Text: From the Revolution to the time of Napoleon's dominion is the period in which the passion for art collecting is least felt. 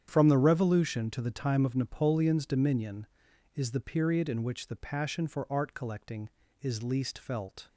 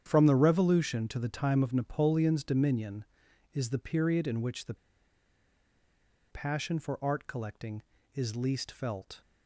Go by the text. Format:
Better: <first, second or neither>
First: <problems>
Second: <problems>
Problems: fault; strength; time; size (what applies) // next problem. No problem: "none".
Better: first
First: starts louder than the rest; strong; until 1.0 s; 9 dB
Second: starts louder than the rest; strong; until 1.0 s; 9 dB // pauses between "the" and "passion"; strong; at 4.7 s; 1.5 s long